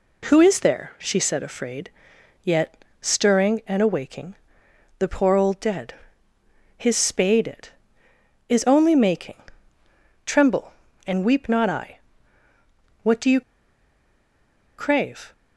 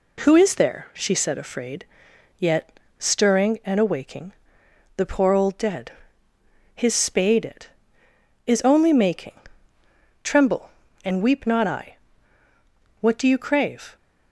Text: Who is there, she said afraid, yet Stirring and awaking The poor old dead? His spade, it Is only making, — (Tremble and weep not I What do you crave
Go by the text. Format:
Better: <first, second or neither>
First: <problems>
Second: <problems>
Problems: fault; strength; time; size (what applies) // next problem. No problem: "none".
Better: second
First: pauses between "yet" and "Stirring"; slight; at 2.8 s; 0.20 s long // pauses between "awaking" and "The"; noticeable; at 4.3 s; 0.62 s long // pauses between "I" and "What"; at 11.9 s; 1.0 s long // pauses between "you" and "crave"; strong; at 13.4 s; 1.3 s long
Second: pauses between "yet" and "Stirring"; slight; at 2.7 s; 0.22 s long // pauses between "awaking" and "The"; noticeable; at 4.3 s; 0.62 s long // pauses between "I" and "What"; at 11.9 s; 1.0 s long